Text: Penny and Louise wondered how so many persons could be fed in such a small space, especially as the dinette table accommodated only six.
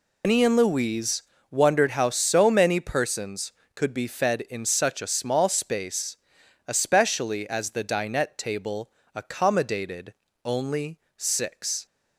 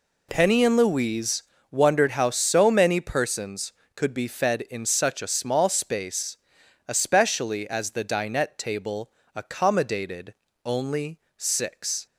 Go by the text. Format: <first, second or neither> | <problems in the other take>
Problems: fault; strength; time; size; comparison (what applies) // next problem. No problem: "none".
second | loses the start of "Penny"; at 0.2 s; 165 ms // pauses between "Louise" and "wondered"; slight; at 1.2 s; 0.30 s long; slight in the second // pauses between "table" and "accommodated"; slight; at 8.9 s; 0.24 s long; slight in the second // pauses between "accommodated" and "only"; slight; at 10.1 s; 0.30 s long; slight in the second // pauses between "only" and "six"; slight; at 10.9 s; 0.16 s long; slight in the second